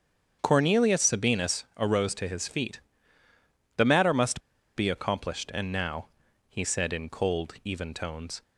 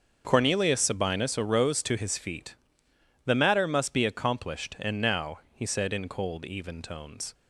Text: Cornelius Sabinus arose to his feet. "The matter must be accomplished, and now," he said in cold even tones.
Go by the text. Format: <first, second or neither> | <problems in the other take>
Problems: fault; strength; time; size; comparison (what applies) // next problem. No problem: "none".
second | starts louder than the rest; strong; until 1.4 s; 7.5 dB; also in the second // pauses between "must" and "be"; slight; at 4.4 s; 0.34 s long